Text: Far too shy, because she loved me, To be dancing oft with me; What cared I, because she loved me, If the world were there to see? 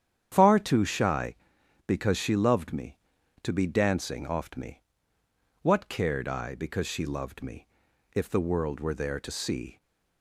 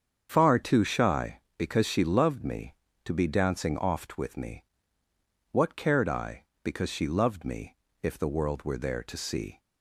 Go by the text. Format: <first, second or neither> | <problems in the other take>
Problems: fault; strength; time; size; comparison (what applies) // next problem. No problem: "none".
second | starts louder than the rest; strong; until 1.3 s; 9 dB; strong in the second // skips "with"; at 4.5 s